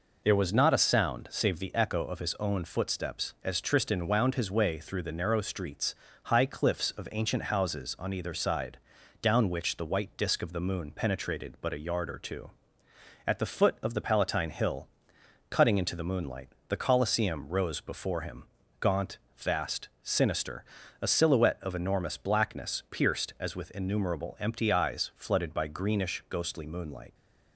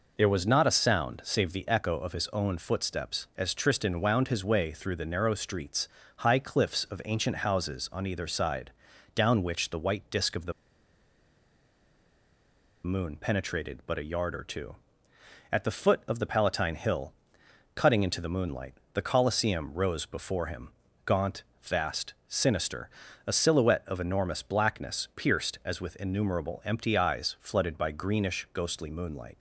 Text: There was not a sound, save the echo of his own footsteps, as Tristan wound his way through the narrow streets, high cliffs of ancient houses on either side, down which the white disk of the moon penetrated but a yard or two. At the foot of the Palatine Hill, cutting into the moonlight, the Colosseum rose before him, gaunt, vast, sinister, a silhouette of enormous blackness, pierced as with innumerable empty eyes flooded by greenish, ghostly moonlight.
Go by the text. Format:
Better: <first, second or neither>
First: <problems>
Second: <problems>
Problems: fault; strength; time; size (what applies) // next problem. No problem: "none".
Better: first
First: none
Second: pauses between "the" and "moon"; strong; at 10.5 s; 2.3 s long